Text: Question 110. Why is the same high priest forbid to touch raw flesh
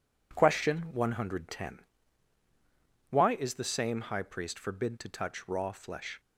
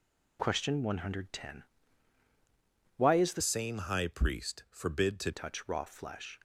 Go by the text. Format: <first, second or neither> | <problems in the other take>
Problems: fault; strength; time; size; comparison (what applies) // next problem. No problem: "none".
first | changes voice from "same" to "to"; from 3.4 to 5.3 s; 1.9 s long